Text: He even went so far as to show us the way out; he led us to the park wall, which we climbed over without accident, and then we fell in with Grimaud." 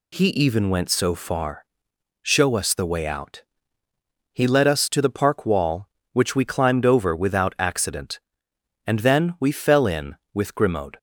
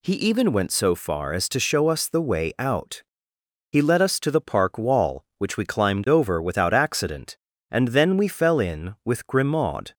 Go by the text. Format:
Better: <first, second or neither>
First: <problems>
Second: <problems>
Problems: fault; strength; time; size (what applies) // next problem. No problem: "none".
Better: second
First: skips "as to"; at 1.9 s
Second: none